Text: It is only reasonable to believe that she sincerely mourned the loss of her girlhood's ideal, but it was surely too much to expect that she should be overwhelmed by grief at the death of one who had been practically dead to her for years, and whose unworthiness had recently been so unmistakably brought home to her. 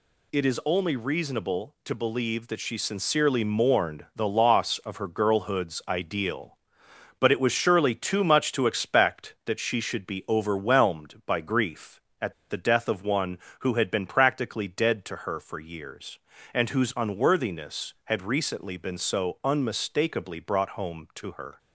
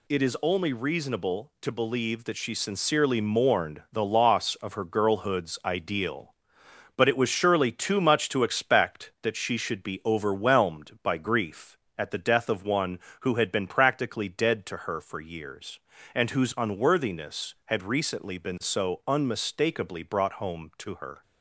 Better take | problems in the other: second | pauses between "at" and "the"; slight; at 12.3 s; 0.16 s long

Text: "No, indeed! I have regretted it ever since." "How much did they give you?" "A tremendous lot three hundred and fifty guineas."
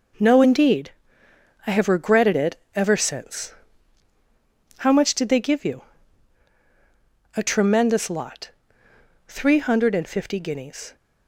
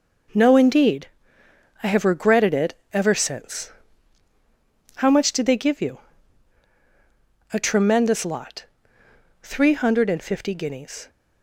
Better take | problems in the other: neither | pauses between "it" and "ever"; slight; the same in both // pauses between "lot" and "three"; noticeable; the same in both

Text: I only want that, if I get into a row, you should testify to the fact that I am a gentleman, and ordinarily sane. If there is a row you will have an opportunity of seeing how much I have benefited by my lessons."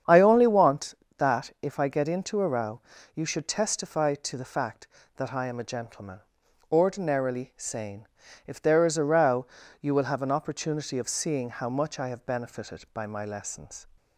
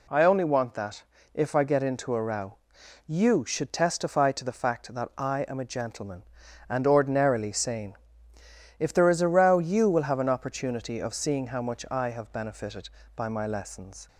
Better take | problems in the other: second | starts louder than the rest; strong; until 1.2 s; 8 dB // skips "and"; at 6.4 s // pauses between "row" and "you"; slight; at 9.4 s; 0.34 s long

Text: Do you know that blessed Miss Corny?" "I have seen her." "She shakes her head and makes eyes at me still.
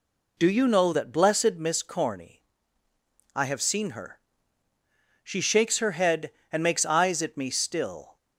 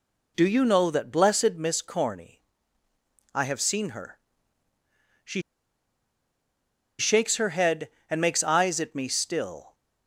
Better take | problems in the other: first | pauses between "She" and "shakes"; strong; at 5.3 s; 1.5 s long

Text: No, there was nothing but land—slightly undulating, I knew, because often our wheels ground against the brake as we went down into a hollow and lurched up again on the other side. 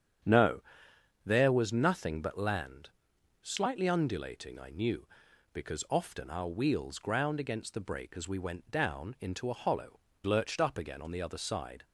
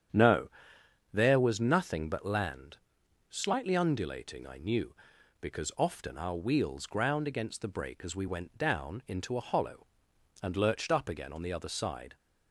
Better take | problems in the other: second | starts louder than the rest; strong; until 1.9 s; 9 dB; strong in the second // skips "and"; at 10.1 s

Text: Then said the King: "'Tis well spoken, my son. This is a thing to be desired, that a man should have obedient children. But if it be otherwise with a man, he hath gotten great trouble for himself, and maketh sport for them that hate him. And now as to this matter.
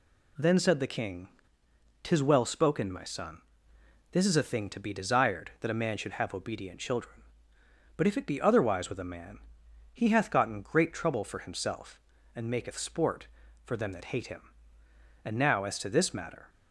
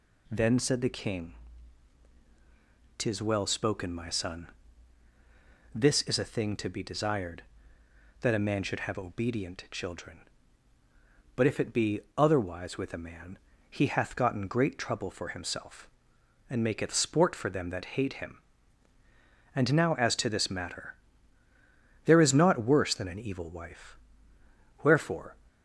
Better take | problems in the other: first | pauses between "be" and "otherwise"; slight; at 12.0 s; 0.16 s long // goes on to say "There is naught worse than an evil wife Wherefore"; strong; from 22.0 s on; 3.3 s long

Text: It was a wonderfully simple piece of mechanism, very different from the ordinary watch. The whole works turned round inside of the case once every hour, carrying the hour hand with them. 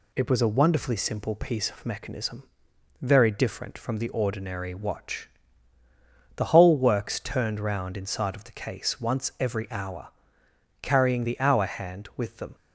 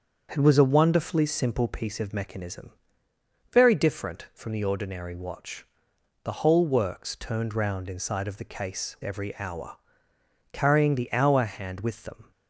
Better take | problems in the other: first | starts louder than the rest; until 1.3 s; 7 dB // skips "once"; at 8.9 s

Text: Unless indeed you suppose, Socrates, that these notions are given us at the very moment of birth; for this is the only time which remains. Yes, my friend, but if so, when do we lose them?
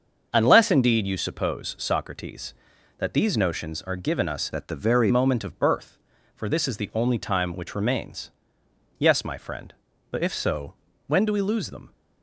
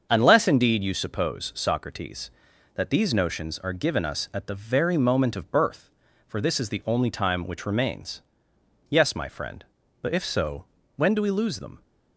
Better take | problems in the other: second | starts louder than the rest; until 1.3 s; 6.5 dB; also in the second // changes voice from "at" to "very"; from 4.5 to 5.1 s; 0.6 s long

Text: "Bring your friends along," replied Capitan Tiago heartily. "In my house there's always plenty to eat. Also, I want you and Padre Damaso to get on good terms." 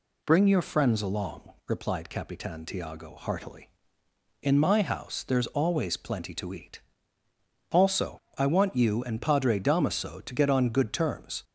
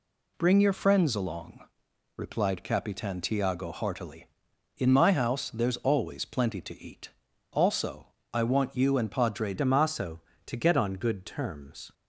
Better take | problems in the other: first | changes voice at "Damaso"; from 9.5 s on; 2.4 s long

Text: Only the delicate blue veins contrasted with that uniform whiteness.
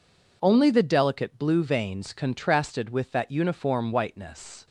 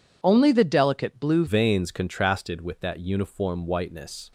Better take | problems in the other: first | changes voice at "veins"; from 1.4 s on; 2.9 s long

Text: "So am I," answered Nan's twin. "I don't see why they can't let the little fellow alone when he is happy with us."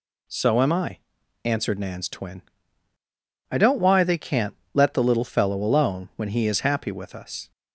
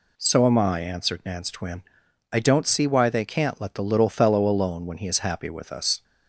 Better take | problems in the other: second | skips "see"; at 3.7 s // pauses between "can't" and "let"; slight; at 4.5 s; 0.18 s long

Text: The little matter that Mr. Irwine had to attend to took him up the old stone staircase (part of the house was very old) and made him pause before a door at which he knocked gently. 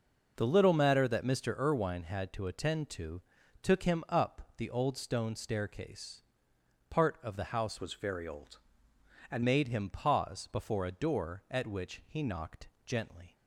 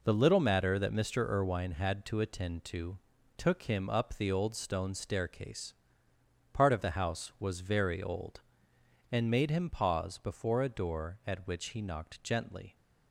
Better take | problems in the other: second | pauses between "to" and "took"; at 3.2 s; 0.40 s long; also in the second // changes voice from "was" to "and"; from 7.8 to 9.4 s; 1.6 s long // pauses between "knocked" and "gently"; slight; at 12.6 s; 0.18 s long

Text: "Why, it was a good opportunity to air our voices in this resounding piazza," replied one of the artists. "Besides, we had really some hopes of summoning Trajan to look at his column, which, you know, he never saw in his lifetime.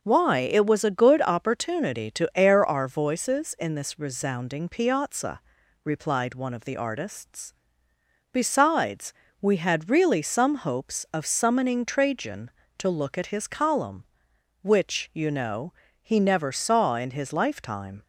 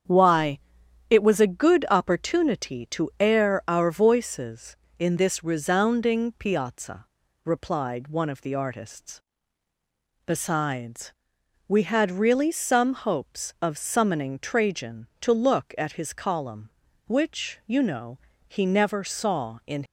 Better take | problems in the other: first | starts louder than the rest; strong; until 1.5 s; 8 dB // stops before "his lifetime"; at 19.8 s

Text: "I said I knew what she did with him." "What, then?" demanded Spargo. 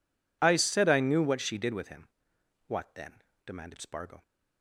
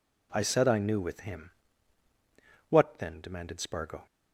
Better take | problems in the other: first | skips "what she did"; at 0.9 s

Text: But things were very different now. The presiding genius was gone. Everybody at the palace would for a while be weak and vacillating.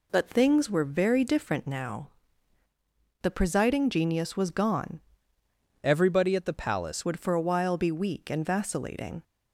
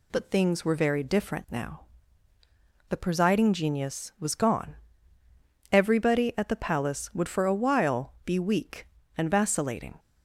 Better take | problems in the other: second | changes voice from "Everybody" to "palace"; from 5.8 to 7.0 s; 1.2 s long

